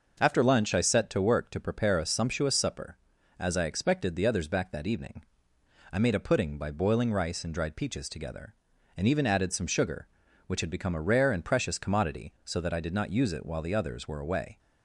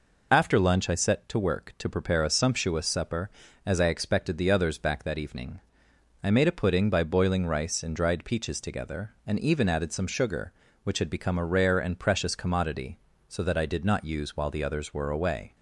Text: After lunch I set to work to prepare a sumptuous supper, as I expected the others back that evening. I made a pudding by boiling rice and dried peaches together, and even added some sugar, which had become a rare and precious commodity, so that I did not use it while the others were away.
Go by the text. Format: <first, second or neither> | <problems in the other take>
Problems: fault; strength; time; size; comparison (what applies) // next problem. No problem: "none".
first | skips "it"; at 14.3 s